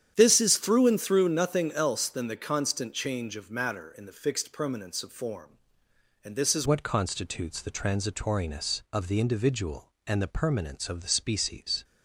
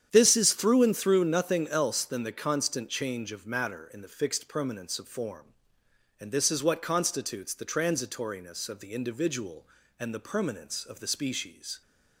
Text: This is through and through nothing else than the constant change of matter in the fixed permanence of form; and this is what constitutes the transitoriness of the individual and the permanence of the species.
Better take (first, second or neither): second